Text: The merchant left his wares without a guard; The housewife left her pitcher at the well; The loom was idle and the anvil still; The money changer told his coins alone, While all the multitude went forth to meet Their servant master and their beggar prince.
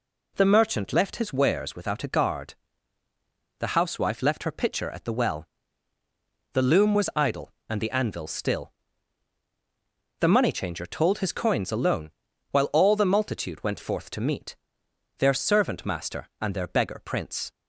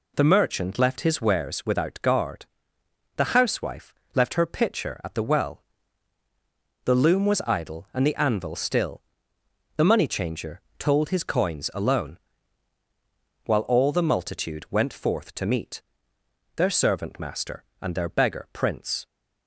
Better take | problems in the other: first | skips "a"; at 2.0 s // pauses between "housewife" and "left"; slight; at 3.9 s; 0.18 s long // pauses between "changer" and "told"; slight; at 10.5 s; 0.18 s long // pauses between "meet" and "Their"; noticeable; at 15.8 s; 0.72 s long; noticeable in the first

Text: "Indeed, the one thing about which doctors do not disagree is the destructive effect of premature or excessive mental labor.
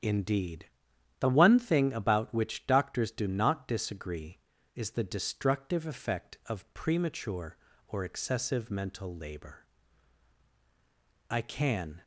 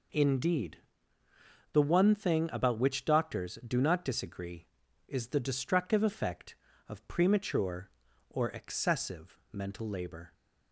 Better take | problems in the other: second | starts louder than the rest; strong; until 1.5 s; 9 dB // goes on to say "I can"; noticeable; from 11.2 s on; 0.74 s long

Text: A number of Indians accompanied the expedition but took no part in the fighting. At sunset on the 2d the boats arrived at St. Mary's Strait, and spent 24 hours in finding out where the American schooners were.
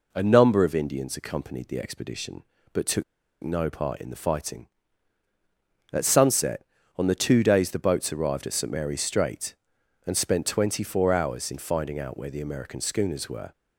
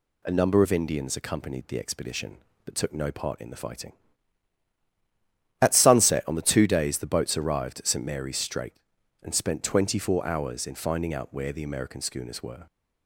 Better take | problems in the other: second | pauses between "took" and "no"; at 3.0 s; 0.40 s long

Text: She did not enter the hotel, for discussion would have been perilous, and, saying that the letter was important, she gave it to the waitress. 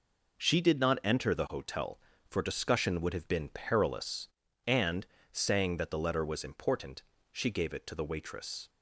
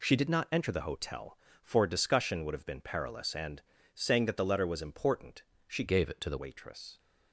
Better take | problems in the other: first | changes voice from "gave" to "the"; from 5.8 to 6.3 s; 0.5 s long

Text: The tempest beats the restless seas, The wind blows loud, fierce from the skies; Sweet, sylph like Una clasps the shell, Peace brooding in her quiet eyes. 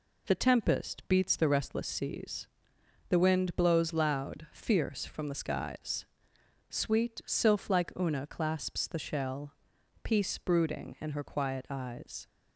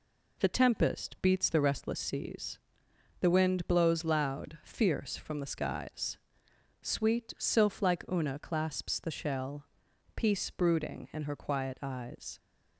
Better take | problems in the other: neither | none

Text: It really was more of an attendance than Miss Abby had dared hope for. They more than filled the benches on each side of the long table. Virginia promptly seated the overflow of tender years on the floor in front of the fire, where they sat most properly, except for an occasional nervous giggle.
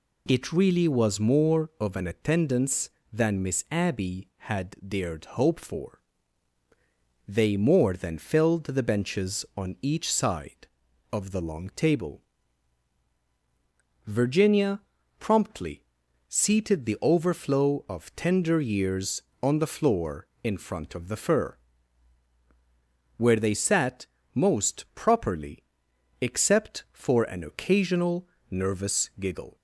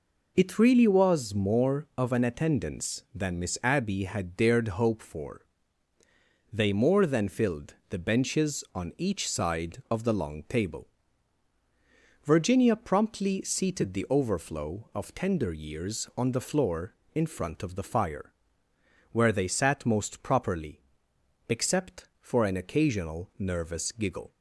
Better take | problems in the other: second | pauses between "Virginia" and "promptly"; at 14.8 s; 0.38 s long // pauses between "promptly" and "seated"; at 15.8 s; 0.44 s long // says "fur" for "fire"; at 21.1 s // pauses between "sat" and "most"; slight; at 24.0 s; 0.30 s long // pauses between "occasional" and "nervous"; slight; at 28.2 s; 0.24 s long

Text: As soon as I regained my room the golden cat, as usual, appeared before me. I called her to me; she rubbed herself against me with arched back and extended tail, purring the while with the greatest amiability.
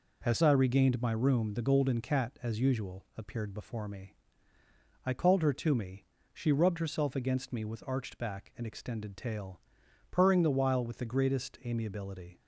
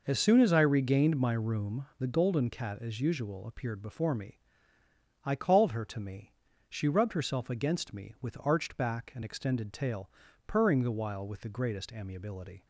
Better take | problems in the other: second | skips "soon as"; at 0.3 s

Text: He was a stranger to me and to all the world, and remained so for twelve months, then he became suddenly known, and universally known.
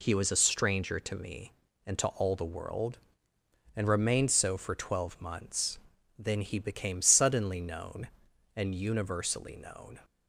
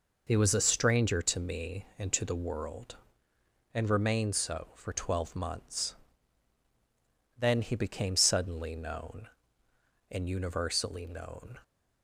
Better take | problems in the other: first | skips "all"; at 2.2 s

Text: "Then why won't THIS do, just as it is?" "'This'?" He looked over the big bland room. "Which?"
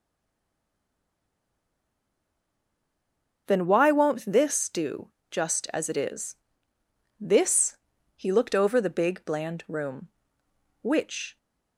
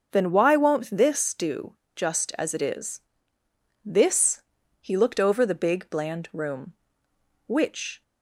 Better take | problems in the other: second | stays silent before the first word; strong; until 3.4 s; 3.4 s long // starts louder than the rest; until 4.4 s; 6.5 dB; also in the second

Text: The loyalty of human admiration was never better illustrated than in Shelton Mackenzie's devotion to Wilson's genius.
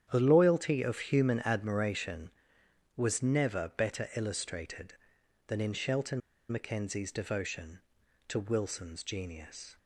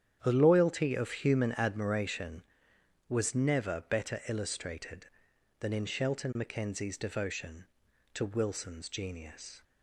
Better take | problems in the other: second | starts louder than the rest; strong; until 1.1 s; 10 dB; strong in the second // pauses between "Shelton" and "Mackenzie's"; slight; at 6.2 s; 0.30 s long

